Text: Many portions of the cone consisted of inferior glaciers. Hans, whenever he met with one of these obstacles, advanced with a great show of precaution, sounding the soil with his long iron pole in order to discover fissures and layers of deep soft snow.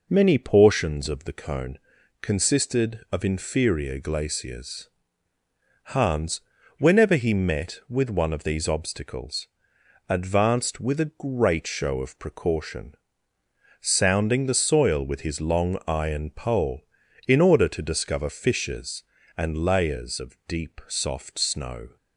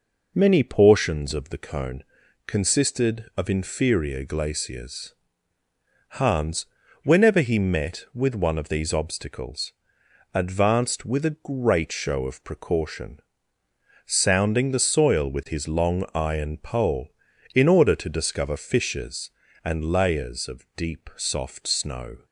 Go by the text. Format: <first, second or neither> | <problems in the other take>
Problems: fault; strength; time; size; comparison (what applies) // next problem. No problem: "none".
neither | pauses between "cone" and "consisted"; the same in both